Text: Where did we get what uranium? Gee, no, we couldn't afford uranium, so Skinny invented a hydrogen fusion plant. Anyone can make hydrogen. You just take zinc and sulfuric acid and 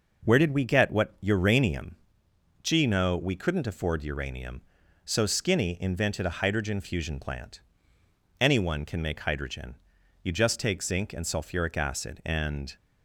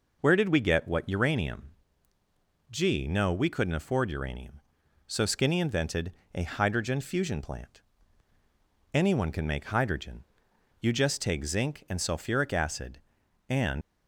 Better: first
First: none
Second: pauses between "invented" and "a"; slight; at 6.1 s; 0.22 s long // leaves "and" unfinished; at 13.8 s; 100 ms

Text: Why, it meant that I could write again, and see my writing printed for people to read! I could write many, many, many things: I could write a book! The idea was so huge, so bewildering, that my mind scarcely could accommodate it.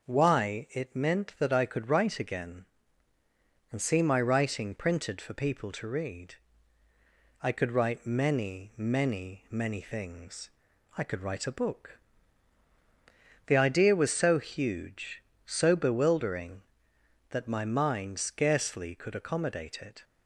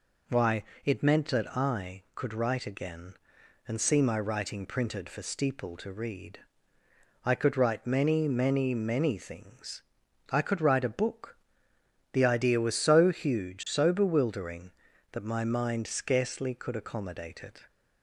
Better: first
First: none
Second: says "steeple" for "people"; at 5.2 s

